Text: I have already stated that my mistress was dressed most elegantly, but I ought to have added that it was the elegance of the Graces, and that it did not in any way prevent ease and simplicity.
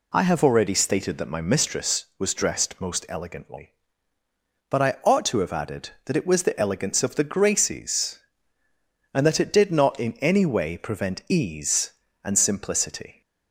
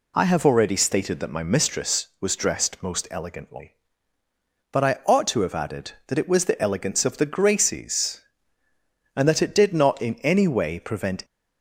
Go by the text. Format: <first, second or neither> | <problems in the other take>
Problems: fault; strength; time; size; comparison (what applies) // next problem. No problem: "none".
first | stops before "ease and simplicity"; at 11.2 s